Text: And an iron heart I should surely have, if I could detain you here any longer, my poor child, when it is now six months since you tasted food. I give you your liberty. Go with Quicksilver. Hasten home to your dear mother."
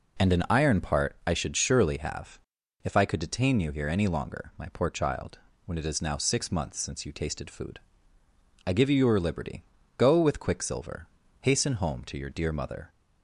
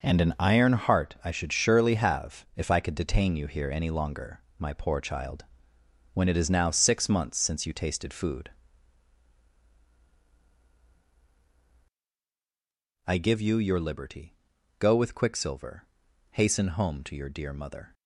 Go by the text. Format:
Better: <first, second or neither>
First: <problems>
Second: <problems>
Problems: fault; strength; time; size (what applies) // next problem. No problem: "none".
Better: second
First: says "part" for "heart"; at 0.7 s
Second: none